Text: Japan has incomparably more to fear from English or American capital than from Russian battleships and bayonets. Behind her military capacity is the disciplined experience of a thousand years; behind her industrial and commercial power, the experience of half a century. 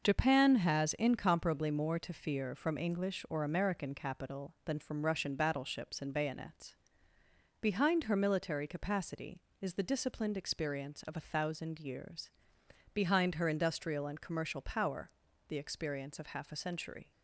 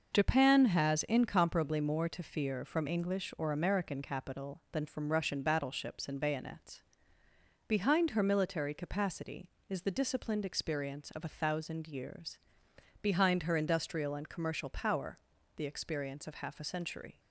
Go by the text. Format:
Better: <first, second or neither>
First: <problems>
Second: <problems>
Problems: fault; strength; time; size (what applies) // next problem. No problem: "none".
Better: neither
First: none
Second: none